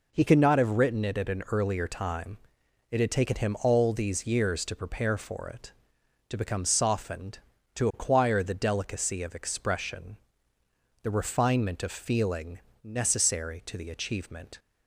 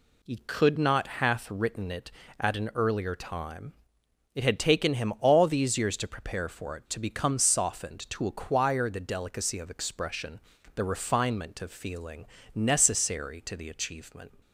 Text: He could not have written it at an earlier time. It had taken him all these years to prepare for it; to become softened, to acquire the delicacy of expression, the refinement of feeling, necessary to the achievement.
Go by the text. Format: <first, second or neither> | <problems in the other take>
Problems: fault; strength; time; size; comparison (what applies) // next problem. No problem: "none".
first | says "hath" for "have"; at 1.0 s